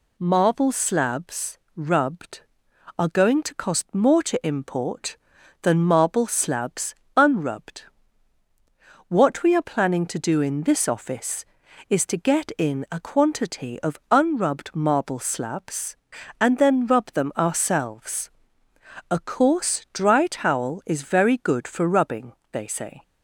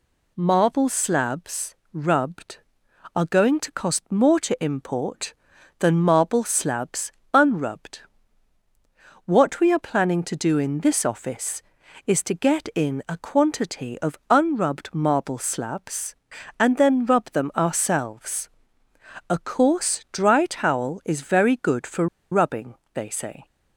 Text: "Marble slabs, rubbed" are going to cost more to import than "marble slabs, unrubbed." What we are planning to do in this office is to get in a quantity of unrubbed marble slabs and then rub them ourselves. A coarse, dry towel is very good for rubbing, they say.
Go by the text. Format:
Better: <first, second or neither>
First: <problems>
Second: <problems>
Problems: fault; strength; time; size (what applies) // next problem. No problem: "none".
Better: first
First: none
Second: pauses between "for" and "rubbing"; slight; at 22.0 s; 0.25 s long